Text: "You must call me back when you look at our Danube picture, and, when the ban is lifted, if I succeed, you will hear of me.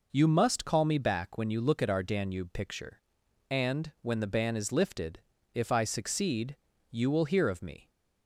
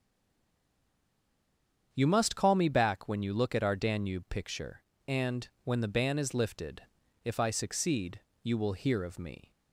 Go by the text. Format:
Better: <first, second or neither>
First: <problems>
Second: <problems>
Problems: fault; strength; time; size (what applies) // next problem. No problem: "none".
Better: first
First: none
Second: stays silent before the first word; noticeable; until 1.9 s; 1.9 s long // starts louder than the rest; strong; until 2.9 s; 8 dB